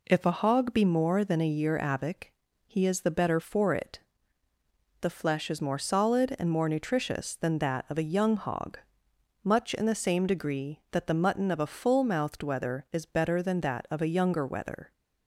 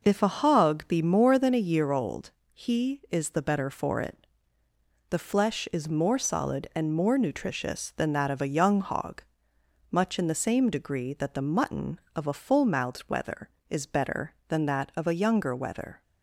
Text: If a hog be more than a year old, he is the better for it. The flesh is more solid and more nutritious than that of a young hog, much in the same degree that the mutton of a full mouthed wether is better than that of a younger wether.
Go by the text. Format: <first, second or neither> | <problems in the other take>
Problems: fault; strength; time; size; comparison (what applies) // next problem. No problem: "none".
second | says "avic" for "old"; at 1.7 s